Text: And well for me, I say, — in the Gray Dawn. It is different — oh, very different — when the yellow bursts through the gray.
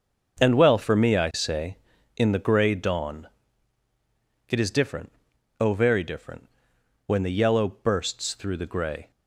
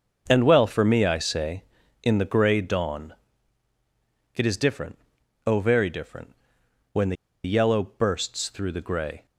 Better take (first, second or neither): first